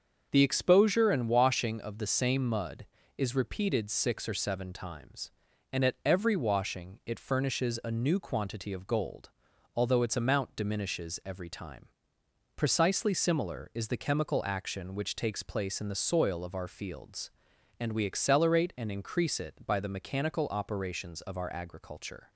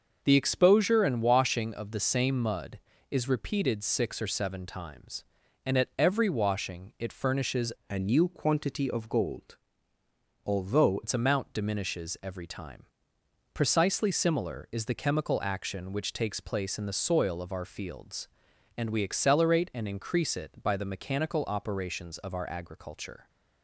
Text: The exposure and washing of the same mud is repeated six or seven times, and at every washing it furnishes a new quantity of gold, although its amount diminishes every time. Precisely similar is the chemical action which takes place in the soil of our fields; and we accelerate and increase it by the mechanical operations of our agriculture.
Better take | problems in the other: first | starts louder than the rest; until 1.2 s; 6 dB; also in the first // changes voice from "a" to "although"; from 7.8 to 11.0 s; 3.2 s long

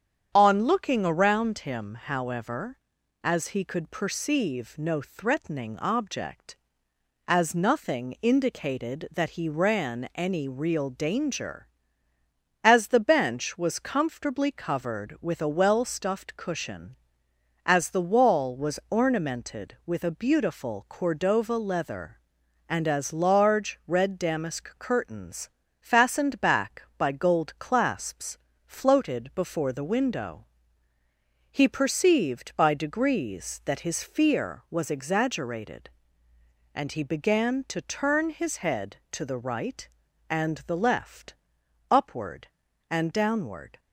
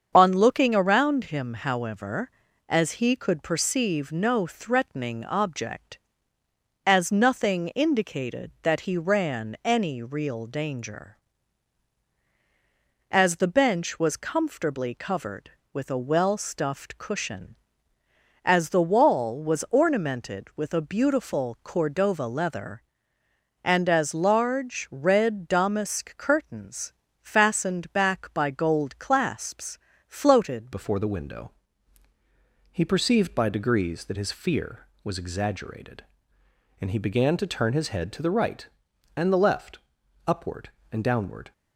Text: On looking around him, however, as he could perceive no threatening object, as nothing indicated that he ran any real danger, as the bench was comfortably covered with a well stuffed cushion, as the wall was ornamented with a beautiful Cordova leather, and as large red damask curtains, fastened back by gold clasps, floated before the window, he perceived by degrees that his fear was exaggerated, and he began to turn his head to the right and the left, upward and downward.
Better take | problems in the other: first | starts louder than the rest; strong; until 1.1 s; 7.5 dB; strong in the first // changes voice at "before"; from 30.7 s on; 10.8 s long

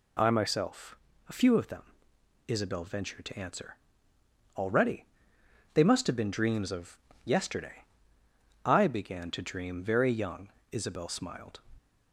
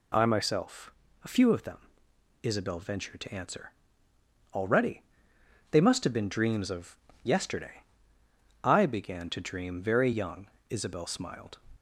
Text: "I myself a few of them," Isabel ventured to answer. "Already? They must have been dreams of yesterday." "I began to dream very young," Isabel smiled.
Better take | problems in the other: neither | pauses between "myself" and "a"; slight; the same in both // pauses between "of" and "yesterday"; slight; the same in both

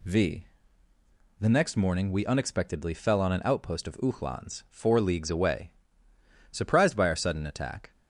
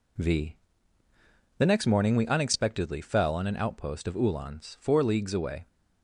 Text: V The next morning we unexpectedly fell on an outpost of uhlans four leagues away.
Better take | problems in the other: second | pauses between "V" and "The"; noticeable; at 0.4 s; 0.92 s long; also in the second // goes on to say "Surprised by our sudden attack"; from 6.4 s on; 1.4 s long

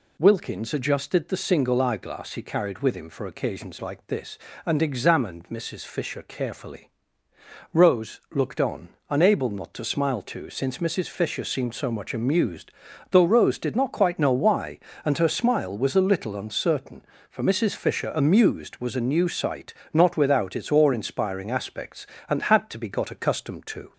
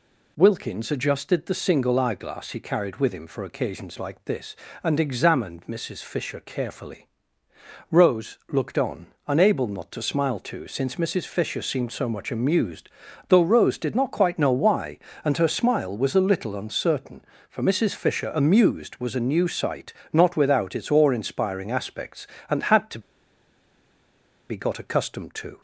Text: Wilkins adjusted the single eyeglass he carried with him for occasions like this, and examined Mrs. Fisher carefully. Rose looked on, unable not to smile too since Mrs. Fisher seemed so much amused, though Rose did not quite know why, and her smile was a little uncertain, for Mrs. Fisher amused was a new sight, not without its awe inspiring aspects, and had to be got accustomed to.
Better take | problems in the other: first | pauses between "to" and "be"; strong; at 22.9 s; 1.5 s long

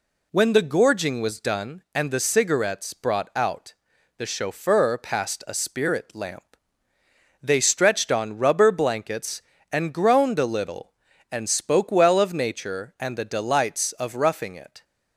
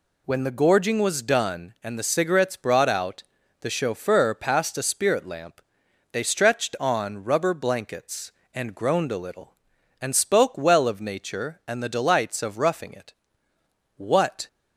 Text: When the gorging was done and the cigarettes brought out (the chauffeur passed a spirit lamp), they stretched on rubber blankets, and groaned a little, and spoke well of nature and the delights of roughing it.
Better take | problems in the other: first | goes on to say "What"; from 13.9 s on; 0.50 s long

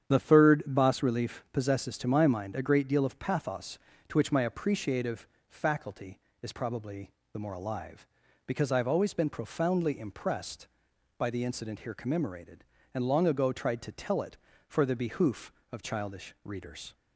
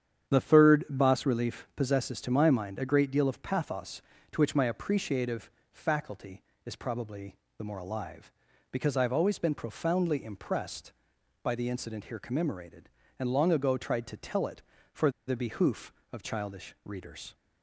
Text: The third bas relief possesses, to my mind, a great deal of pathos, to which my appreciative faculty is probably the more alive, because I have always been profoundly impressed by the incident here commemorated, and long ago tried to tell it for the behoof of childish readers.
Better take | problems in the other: first | starts louder than the rest; strong; until 1.3 s; 9 dB; strong in the first // pauses between "appreciative" and "faculty"; slight; at 5.4 s; 0.22 s long; slight in the first // pauses between "probably" and "the"; slight; at 7.3 s; 0.20 s long; slight in the first // pauses between "for" and "the"; slight; at 15.0 s; 0.18 s long

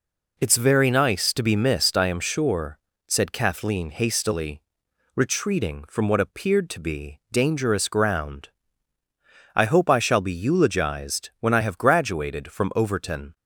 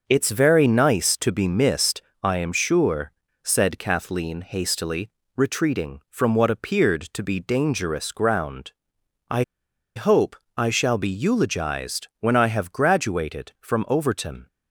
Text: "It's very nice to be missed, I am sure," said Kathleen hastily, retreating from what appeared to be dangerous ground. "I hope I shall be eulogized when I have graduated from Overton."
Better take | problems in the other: first | pauses between "I" and "hope"; noticeable; at 9.4 s; 0.54 s long // pauses between "hope" and "I"; slight; at 10.3 s; 0.22 s long

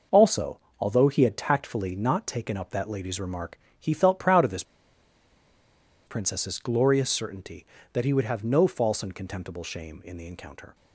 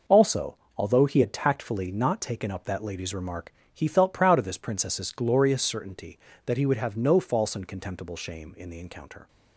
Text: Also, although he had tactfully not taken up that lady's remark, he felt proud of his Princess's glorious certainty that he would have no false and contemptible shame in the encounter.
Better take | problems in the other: second | pauses between "his" and "Princess's"; strong; at 4.6 s; 1.4 s long

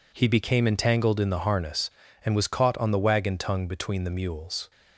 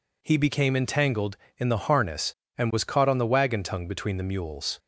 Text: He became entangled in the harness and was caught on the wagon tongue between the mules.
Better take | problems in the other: neither | none

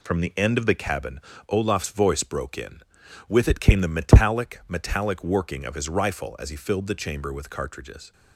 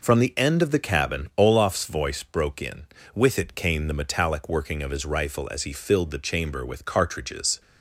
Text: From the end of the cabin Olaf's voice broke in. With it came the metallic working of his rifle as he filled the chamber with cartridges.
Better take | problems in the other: second | pauses between "cabin" and "Olaf's"; slight; at 1.1 s; 0.28 s long // says "metallic" twice; at 4.6 s

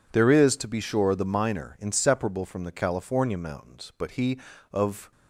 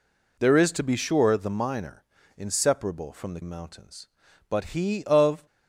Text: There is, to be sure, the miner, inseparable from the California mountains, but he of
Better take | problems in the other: first | skips "California"; at 3.4 s

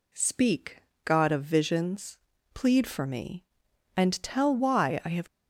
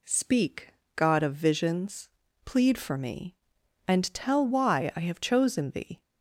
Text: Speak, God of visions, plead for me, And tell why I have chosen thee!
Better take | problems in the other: second | stops before "chosen thee"; at 5.2 s

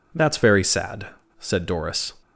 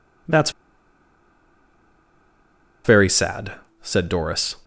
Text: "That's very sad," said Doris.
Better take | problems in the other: first | pauses between "That's" and "very"; strong; at 0.5 s; 2.3 s long

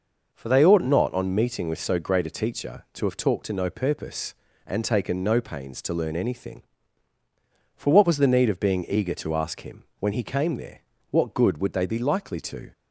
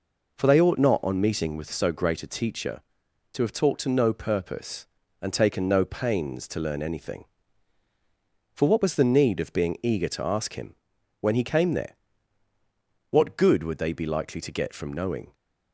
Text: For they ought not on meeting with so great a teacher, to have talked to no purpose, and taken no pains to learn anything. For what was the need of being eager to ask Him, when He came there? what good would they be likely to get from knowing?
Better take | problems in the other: second | stops before "get from knowing"; at 12.7 s

